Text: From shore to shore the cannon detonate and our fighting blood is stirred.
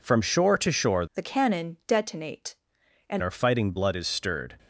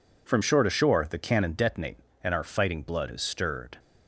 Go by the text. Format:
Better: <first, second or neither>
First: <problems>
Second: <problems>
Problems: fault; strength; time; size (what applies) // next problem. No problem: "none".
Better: second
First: changes voice from "the" to "and"; from 1.1 to 3.2 s; 2.1 s long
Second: none